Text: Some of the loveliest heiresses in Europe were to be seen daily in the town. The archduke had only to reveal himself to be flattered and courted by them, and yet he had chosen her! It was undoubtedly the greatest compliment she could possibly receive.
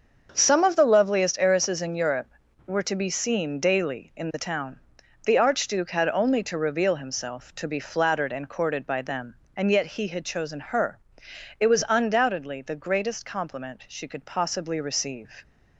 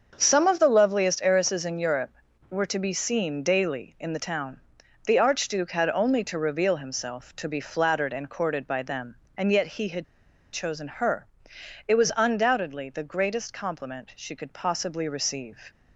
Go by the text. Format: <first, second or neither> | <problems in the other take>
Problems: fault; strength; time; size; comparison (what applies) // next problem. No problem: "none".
first | starts louder than the rest; until 1.1 s; 6.5 dB; also in the first // pauses between "had" and "chosen"; noticeable; at 10.0 s; 0.47 s long